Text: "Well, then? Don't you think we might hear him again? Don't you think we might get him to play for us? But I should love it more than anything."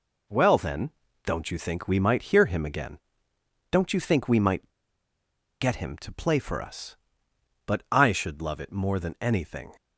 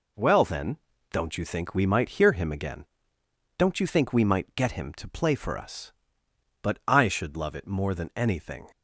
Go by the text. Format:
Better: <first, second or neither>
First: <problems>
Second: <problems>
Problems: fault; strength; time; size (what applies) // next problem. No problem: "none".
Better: second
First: pauses between "might" and "get"; noticeable; at 4.6 s; 0.89 s long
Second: none